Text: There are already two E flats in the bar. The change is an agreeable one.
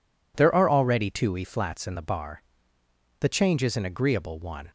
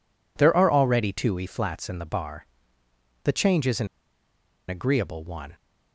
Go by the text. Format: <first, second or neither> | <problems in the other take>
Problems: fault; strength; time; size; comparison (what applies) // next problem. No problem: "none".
first | pauses between "an" and "agreeable"; noticeable; at 3.8 s; 0.82 s long